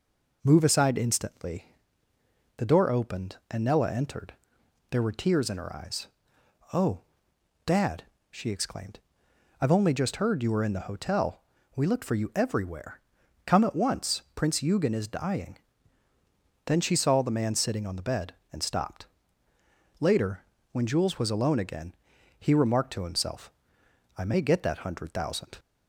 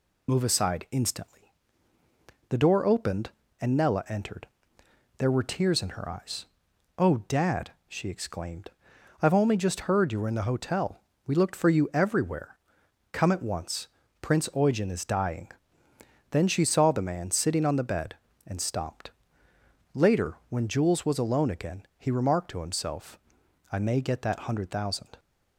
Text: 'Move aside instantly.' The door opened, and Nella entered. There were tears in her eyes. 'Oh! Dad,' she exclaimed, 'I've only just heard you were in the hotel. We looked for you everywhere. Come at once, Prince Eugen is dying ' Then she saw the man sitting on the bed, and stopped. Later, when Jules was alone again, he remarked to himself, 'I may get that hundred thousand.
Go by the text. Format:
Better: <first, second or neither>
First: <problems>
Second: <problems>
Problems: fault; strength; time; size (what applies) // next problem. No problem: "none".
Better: first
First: none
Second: loses the start of "Move"; at 0.2 s; 35 ms